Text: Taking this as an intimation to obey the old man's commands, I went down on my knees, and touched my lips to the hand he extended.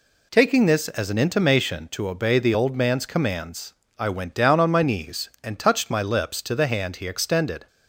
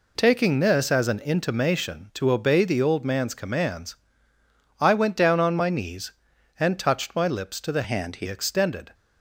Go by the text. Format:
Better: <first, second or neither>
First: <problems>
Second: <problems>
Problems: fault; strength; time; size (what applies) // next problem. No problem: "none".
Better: first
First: none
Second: changes voice from "hand" to "he"; from 7.8 to 8.2 s; 0.4 s long